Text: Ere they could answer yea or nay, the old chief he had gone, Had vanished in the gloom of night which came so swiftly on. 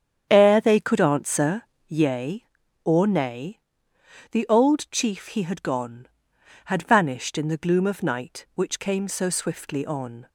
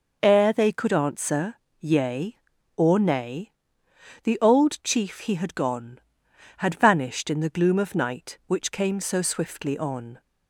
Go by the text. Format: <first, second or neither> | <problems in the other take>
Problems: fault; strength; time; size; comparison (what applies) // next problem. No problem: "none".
second | starts louder than the rest; strong; until 2.1 s; 8.5 dB // pauses between "answer" and "yea"; slight; at 1.6 s; 0.26 s long; slight in the second